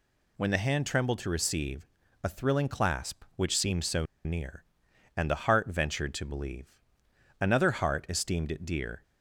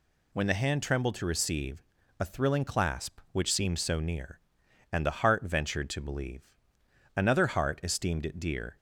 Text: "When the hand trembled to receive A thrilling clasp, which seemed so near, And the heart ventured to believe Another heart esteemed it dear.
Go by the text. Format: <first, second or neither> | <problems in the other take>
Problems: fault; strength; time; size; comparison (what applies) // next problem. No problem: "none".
second | pauses between "receive" and "A"; slight; at 1.8 s; 0.36 s long; slight in the second // pauses between "so" and "near"; slight; at 4.0 s; 0.21 s long // pauses between "believe" and "Another"; noticeable; at 6.7 s; 0.64 s long; noticeable in the second